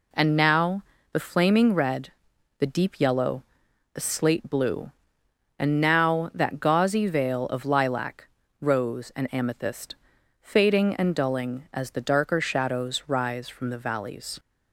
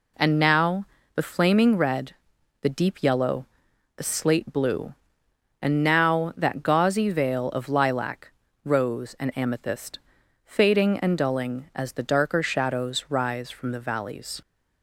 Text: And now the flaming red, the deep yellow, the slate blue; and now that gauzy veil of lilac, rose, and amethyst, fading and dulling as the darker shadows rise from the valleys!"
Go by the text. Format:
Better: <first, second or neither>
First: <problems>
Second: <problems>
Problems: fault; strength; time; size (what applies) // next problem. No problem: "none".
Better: neither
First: pauses between "now" and "the"; slight; at 0.8 s; 0.30 s long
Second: pauses between "now" and "the"; slight; at 0.8 s; 0.30 s long